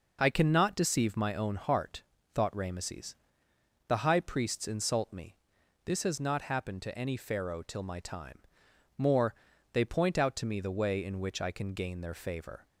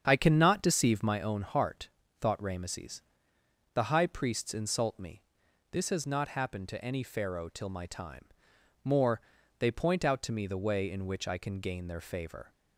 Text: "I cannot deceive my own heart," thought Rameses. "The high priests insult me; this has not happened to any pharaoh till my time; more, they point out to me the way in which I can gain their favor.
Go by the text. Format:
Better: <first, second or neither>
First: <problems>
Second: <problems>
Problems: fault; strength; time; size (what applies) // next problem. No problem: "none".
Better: first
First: none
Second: starts louder than the rest; strong; until 1.2 s; 8 dB